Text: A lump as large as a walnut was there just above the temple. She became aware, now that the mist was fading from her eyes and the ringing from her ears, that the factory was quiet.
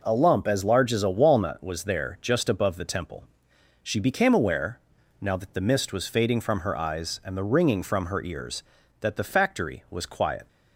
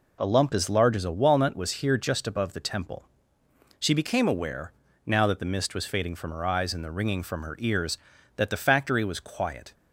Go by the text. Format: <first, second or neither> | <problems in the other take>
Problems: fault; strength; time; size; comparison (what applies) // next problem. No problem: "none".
first | says "here" for "there"; at 1.7 s